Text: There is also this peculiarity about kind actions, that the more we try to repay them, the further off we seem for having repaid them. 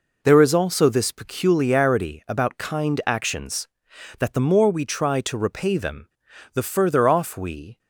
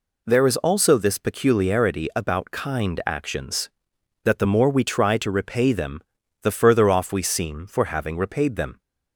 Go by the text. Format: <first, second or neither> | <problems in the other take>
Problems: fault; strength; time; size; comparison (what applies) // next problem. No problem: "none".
second | stops before "seem for having repaid them"; at 7.7 s